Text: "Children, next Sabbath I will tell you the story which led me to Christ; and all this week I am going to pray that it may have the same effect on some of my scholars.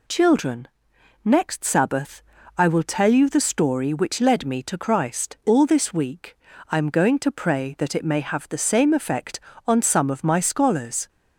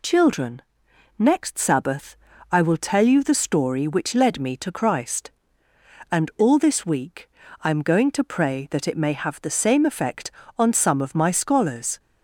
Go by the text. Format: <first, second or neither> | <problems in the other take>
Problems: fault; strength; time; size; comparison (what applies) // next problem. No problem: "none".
second | pauses between "Sabbath" and "I"; slight; at 2.2 s; 0.36 s long; slight in the second // skips "and"; at 5.4 s // pauses between "week" and "I"; slight; at 6.3 s; 0.34 s long; slight in the second